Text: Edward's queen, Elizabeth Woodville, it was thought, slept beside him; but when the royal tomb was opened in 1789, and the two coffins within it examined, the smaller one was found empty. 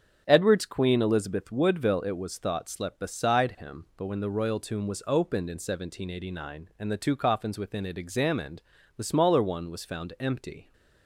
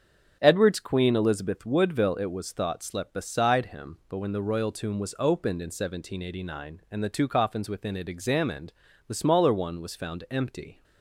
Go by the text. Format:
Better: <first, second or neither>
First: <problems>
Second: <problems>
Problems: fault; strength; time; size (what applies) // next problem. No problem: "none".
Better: neither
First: starts louder than the rest; strong; until 1.2 s; 7 dB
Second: starts louder than the rest; strong; until 1.4 s; 7 dB